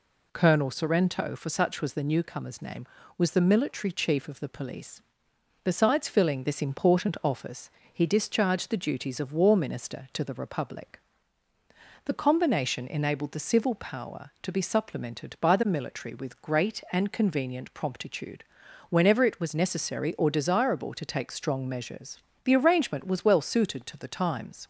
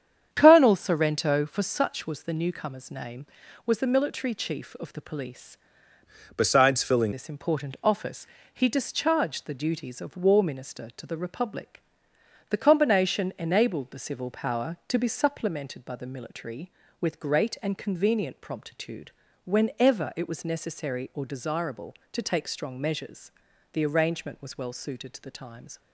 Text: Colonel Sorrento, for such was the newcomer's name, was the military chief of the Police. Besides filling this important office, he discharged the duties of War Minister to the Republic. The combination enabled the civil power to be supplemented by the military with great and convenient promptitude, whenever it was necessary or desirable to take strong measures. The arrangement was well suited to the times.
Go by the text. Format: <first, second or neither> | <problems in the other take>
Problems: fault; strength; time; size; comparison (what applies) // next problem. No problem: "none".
first | starts louder than the rest; strong; until 1.3 s; 8.5 dB // changes voice from "Besides" to "filling"; from 6.3 to 7.1 s; 0.8 s long